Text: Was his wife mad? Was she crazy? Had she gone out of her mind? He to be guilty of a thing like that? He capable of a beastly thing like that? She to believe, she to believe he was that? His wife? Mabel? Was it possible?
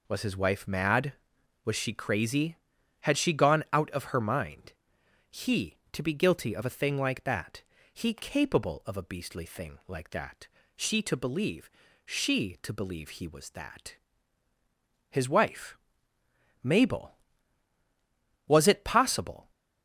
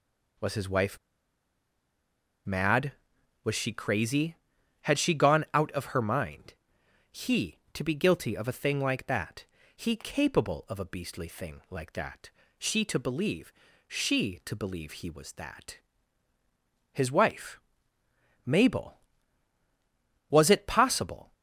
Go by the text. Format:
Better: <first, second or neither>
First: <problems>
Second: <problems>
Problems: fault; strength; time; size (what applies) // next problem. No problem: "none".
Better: first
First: none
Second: pauses between "wife" and "mad"; strong; at 0.9 s; 1.4 s long